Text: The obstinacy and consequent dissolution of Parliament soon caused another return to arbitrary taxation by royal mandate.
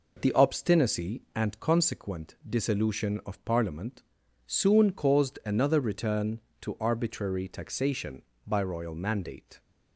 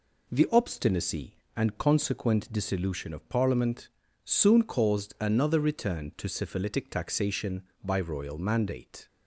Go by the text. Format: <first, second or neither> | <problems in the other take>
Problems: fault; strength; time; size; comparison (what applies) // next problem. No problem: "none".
first | pauses between "Parliament" and "soon"; at 3.8 s; 0.38 s long; noticeable in the first // says "syphilitic" for "arbitrary"; at 6.2 s